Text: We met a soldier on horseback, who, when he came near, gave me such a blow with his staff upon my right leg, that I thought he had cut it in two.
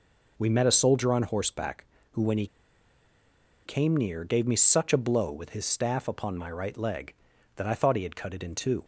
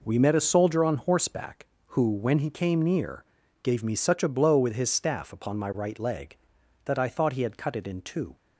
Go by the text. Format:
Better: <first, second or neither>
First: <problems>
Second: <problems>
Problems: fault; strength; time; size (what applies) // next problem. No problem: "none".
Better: second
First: pauses between "he" and "came"; at 2.4 s; 1.1 s long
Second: none